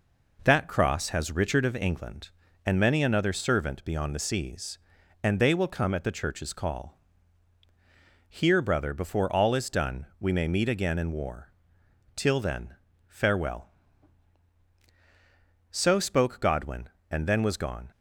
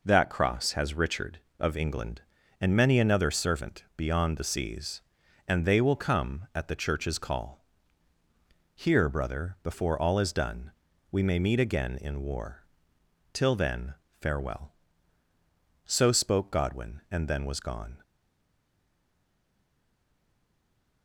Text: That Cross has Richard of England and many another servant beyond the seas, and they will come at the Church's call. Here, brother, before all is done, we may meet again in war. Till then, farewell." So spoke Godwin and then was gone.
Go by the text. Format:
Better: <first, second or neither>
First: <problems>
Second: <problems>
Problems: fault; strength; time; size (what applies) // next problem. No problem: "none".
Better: first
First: none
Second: stays silent after the last word; strong; from 18.0 s on; 3.0 s long